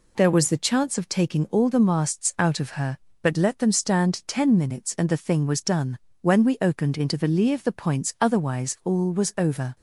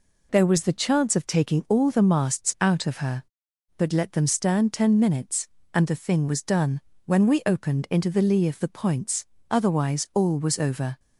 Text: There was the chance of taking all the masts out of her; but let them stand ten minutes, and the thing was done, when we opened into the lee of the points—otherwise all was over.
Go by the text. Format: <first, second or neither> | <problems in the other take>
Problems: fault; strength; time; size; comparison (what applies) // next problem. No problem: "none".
neither | none